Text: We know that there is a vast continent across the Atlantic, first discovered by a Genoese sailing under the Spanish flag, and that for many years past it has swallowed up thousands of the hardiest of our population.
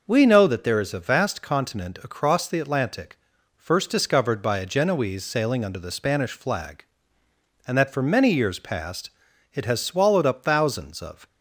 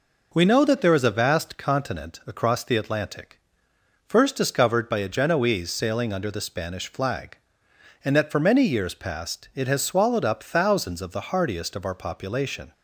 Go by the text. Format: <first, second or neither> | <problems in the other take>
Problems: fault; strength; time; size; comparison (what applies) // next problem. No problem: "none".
second | pauses between "past" and "it"; at 9.1 s; 0.42 s long // stops before "the hardiest of our population"; at 11.2 s